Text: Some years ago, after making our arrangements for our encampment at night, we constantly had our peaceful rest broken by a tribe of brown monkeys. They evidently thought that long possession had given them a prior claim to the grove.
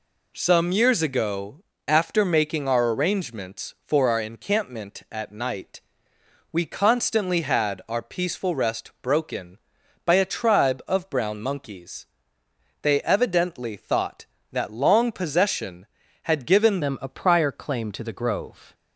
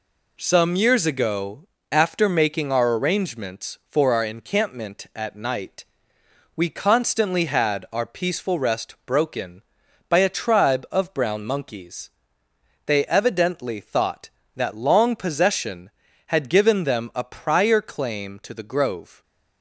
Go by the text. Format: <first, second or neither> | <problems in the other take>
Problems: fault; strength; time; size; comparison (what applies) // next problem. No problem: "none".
second | changes voice at "them"; from 16.8 s on; 1.9 s long